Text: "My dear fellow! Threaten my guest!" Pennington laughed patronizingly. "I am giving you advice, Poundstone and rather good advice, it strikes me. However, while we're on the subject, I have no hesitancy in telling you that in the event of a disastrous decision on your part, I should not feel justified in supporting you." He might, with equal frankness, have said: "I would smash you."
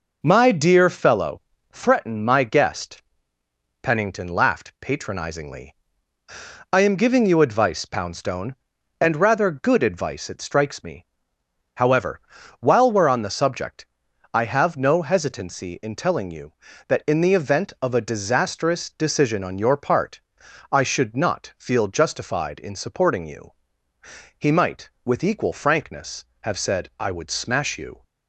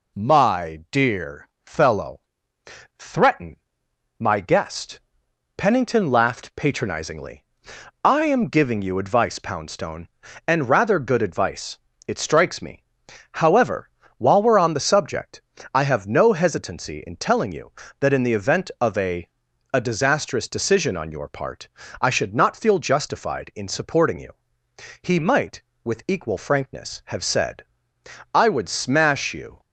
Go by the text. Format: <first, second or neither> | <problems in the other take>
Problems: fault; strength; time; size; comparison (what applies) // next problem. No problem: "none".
first | pauses between "dear" and "fellow"; slight; at 1.4 s; 0.16 s long // pauses between "Threaten" and "my"; noticeable; at 3.5 s; 0.62 s long // says "a" twice; at 19.7 s